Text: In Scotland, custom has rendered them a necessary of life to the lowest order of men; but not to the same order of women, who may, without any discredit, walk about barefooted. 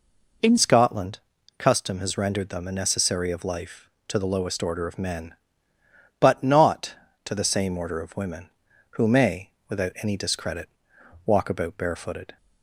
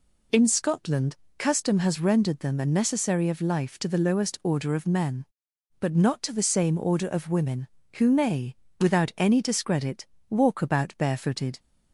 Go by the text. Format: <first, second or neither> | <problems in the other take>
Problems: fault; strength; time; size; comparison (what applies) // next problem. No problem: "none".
second | changes voice at "Scotland"; from 0.5 s on; 11.8 s long